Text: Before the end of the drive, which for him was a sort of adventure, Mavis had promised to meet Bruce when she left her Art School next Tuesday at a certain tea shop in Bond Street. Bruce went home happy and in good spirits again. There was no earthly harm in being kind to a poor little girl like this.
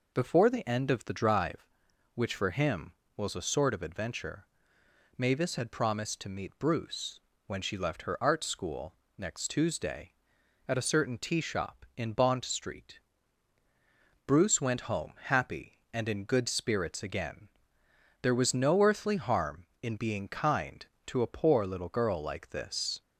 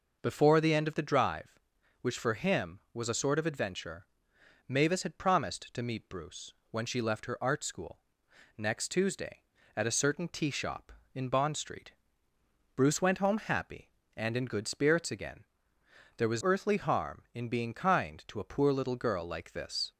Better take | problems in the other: first | pauses between "Bruce" and "when"; slight; at 6.5 s; 0.18 s long; slight in the first // pauses between "School" and "next"; noticeable; at 7.9 s; 0.58 s long; slight in the first // skips "no"; at 16.4 s

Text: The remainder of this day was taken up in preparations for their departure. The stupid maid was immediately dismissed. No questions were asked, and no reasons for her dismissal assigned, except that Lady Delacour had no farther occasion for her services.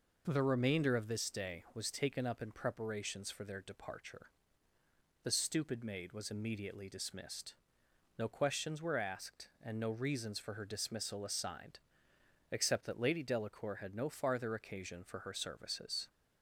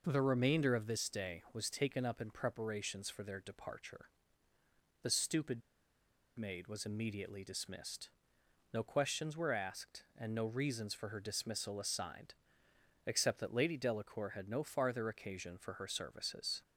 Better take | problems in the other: first | pauses between "stupid" and "maid"; noticeable; at 5.6 s; 0.78 s long

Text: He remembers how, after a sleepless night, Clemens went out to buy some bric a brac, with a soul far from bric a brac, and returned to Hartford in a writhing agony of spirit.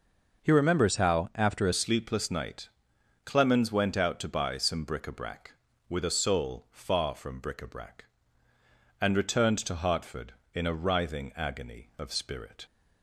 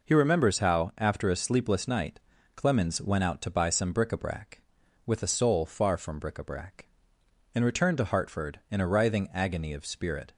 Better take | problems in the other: second | changes voice at "sleepless"; from 1.7 s on; 10.9 s long

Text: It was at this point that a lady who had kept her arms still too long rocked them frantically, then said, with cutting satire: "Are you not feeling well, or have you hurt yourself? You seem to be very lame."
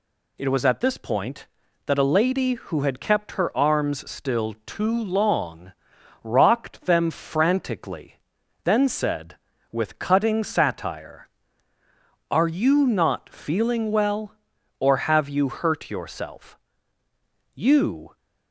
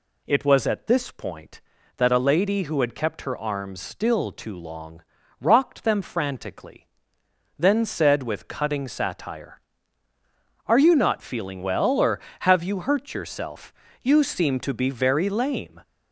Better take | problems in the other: second | pauses between "long" and "rocked"; noticeable; at 5.7 s; 0.52 s long; slight in the second // stops before "seem to be very lame"; at 18.1 s

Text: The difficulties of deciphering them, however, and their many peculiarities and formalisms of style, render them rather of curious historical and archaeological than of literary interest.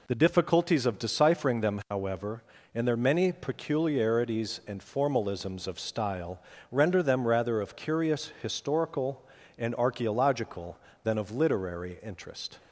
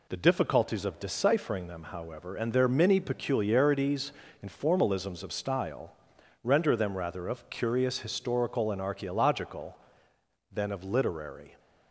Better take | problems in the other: first | stops before "interest"; at 11.5 s

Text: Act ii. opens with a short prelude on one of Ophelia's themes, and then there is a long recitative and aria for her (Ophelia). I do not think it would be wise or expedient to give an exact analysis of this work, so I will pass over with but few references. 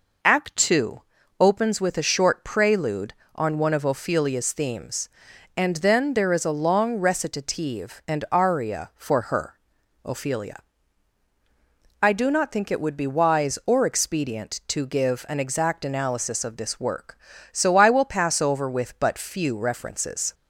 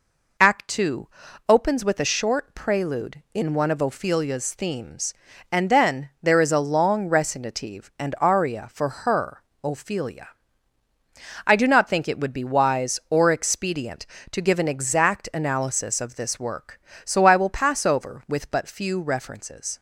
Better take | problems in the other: first | says "in" for "on"; at 3.3 s

